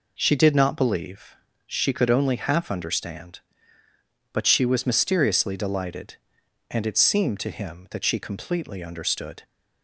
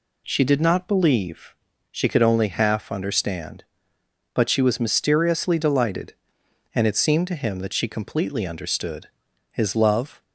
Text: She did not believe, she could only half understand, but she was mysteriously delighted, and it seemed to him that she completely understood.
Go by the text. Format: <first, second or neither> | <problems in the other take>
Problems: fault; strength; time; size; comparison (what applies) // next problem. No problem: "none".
first | goes on to say "His love"; noticeable; from 9.5 s on; 0.70 s long